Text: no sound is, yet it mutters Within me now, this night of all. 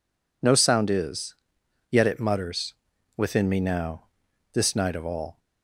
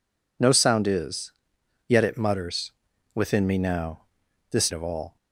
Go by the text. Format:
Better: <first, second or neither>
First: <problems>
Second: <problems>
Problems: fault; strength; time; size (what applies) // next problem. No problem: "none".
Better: first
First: pauses between "mutters" and "Within"; at 2.7 s; 0.44 s long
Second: pauses between "mutters" and "Within"; at 2.7 s; 0.44 s long // skips "night"; at 4.7 s